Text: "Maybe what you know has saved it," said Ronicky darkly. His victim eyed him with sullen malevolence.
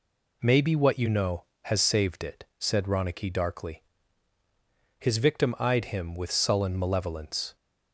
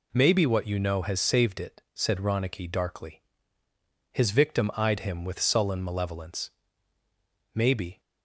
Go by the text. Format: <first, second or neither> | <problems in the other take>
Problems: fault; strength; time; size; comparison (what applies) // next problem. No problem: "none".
first | goes on to say "Maybe"; slight; from 7.5 s on; 0.46 s long